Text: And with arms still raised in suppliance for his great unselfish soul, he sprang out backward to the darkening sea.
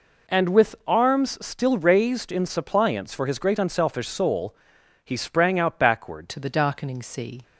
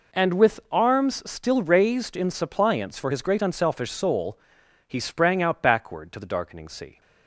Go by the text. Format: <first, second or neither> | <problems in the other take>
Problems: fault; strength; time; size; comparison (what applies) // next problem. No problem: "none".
second | changes voice at "to"; from 6.2 s on; 1.2 s long